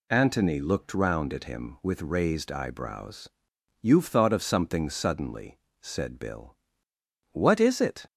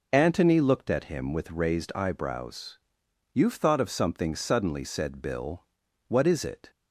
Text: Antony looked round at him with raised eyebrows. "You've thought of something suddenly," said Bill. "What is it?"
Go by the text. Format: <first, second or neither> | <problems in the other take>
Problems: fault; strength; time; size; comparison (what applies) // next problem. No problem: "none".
first | skips "round"; at 0.8 s